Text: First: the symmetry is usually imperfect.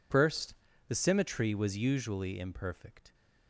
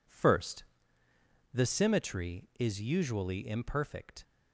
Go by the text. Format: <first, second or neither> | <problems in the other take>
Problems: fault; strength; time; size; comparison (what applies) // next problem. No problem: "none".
second | says "was" for "is"; at 1.5 s